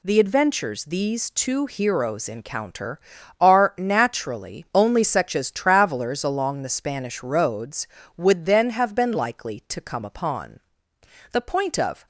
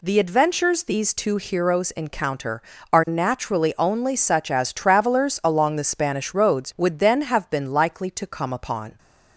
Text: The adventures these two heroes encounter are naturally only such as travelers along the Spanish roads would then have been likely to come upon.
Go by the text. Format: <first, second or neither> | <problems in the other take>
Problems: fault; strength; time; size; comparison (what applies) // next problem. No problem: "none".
second | goes on to say "The point of"; noticeable; from 11.3 s on; 0.74 s long